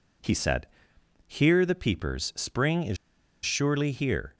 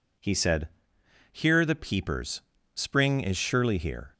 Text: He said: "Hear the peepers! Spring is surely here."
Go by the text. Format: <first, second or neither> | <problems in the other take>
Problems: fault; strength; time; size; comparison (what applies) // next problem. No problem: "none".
second | pauses between "is" and "surely"; noticeable; at 2.9 s; 0.48 s long